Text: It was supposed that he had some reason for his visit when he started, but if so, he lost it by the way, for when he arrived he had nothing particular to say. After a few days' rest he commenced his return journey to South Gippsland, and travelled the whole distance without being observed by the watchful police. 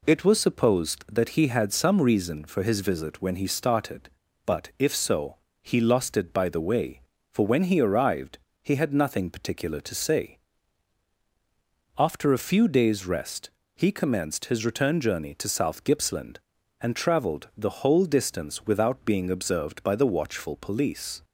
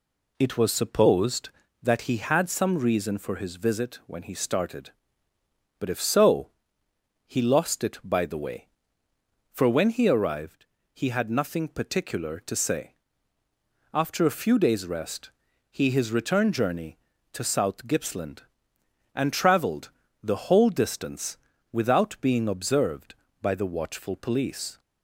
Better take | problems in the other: first | pauses between "arrived" and "he"; slight; at 10.6 s; 0.28 s long; slight in the first // pauses between "rest" and "he"; at 15.3 s; 0.40 s long; slight in the first // skips "commenced"; at 15.8 s // pauses between "travelled" and "the"; slight; at 19.8 s; 0.32 s long // pauses between "distance" and "without"; slight; at 21.3 s; 0.34 s long

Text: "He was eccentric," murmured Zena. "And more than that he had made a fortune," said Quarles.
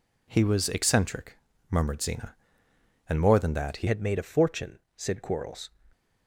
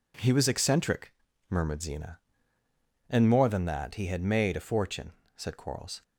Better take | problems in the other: second | changes voice at "had"; from 3.8 s on; 1.8 s long

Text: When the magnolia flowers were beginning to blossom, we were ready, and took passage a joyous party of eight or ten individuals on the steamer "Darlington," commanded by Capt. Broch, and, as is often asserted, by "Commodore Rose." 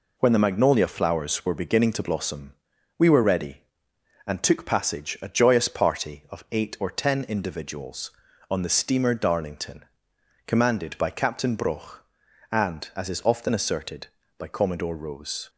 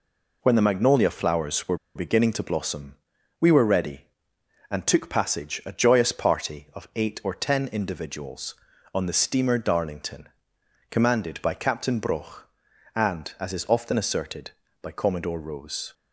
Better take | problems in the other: first | pauses between "were" and "beginning"; slight; at 1.7 s; 0.19 s long

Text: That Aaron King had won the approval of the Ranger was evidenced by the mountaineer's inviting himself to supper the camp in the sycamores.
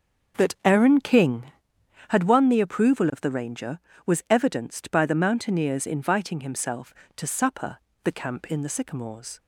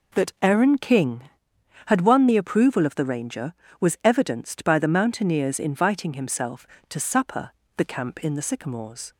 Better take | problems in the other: second | starts louder than the rest; until 2.1 s; 6.5 dB // pauses between "supper" and "the"; slight; at 7.7 s; 0.26 s long; slight in the second

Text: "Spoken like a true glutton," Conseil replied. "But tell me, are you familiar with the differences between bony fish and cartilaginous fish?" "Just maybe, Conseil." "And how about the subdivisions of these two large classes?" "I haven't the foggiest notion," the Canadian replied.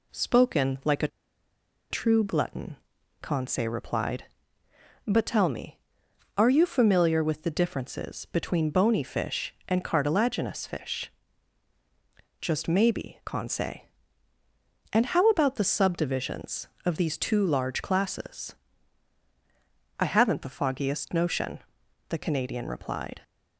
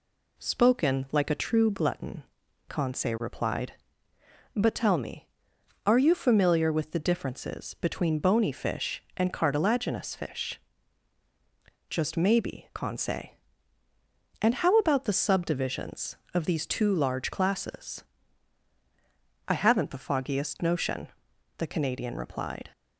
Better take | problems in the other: second | pauses between "a" and "true"; noticeable; at 1.0 s; 0.83 s long

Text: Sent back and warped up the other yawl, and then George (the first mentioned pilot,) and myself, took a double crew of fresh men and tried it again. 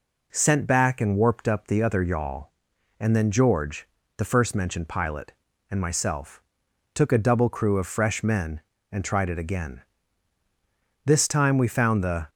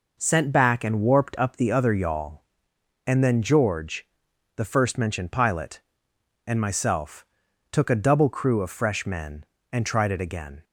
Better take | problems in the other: second | goes on to say "This time we found the"; noticeable; from 11.0 s on; 1.2 s long

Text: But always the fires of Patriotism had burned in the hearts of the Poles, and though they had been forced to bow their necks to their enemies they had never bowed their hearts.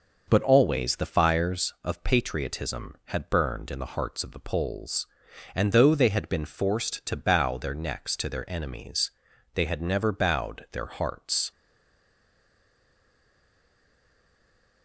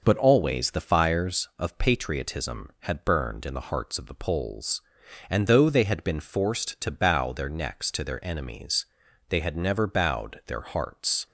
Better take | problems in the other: second | pauses between "enemies" and "they"; at 9.1 s; 0.44 s long; also in the second // stays silent after the last word; strong; from 11.5 s on; 3.3 s long

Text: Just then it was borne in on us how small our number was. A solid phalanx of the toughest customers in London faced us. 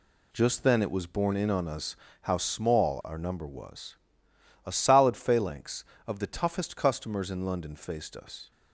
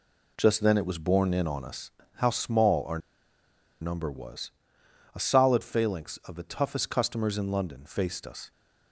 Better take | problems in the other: first | pauses between "us" and "how"; slight; at 1.9 s; 0.26 s long; slight in the first // pauses between "our" and "number"; noticeable; at 2.9 s; 0.82 s long

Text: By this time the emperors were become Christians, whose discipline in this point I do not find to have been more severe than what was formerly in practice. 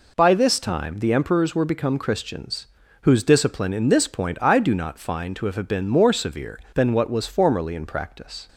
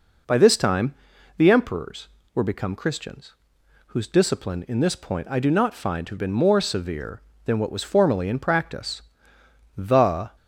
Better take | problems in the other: first | pauses between "time" and "the"; at 0.9 s; 0.44 s long // goes on to say "The"; from 9.7 s on; 0.58 s long

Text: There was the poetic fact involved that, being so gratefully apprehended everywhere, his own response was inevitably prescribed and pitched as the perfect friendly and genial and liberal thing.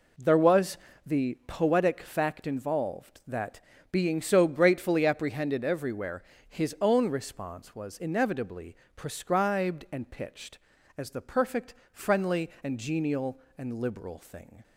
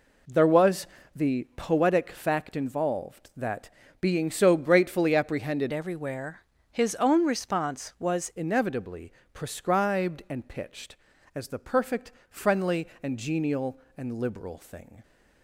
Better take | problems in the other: first | pauses between "was" and "the"; slight; at 0.8 s; 0.26 s long; slight in the first // changes voice from "everywhere" to "was"; from 5.7 to 8.3 s; 2.6 s long // pauses between "inevitably" and "prescribed"; slight; at 9.1 s; 0.20 s long; slight in the first // pauses between "perfect" and "friendly"; slight; at 12.1 s; 0.20 s long; slight in the first

